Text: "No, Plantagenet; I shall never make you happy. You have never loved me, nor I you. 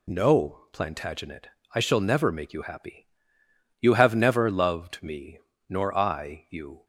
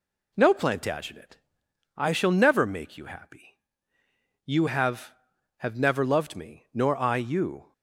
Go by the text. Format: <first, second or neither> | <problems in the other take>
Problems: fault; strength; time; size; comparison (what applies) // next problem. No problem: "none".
first | says "have" twice; at 5.5 s